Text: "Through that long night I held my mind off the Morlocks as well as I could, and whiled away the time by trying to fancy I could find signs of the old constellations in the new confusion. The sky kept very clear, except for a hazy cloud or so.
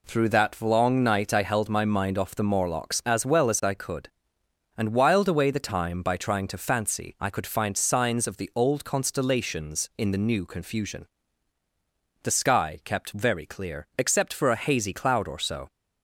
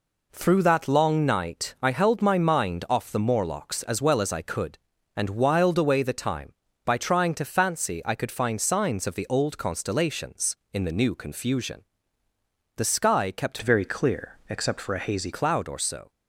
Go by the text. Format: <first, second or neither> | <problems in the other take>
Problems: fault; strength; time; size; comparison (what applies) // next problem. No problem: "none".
first | changes voice from "very" to "hazy"; from 13.6 to 15.3 s; 1.7 s long